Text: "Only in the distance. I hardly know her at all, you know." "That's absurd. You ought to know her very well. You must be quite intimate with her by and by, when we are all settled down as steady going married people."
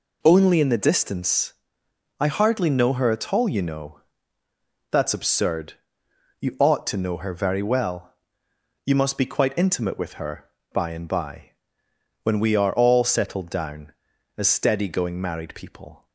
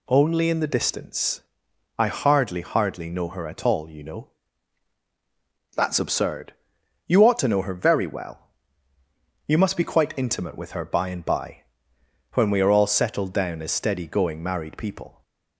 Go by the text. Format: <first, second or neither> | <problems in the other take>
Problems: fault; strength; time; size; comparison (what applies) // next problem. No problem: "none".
first | says "hardly" twice; at 2.6 s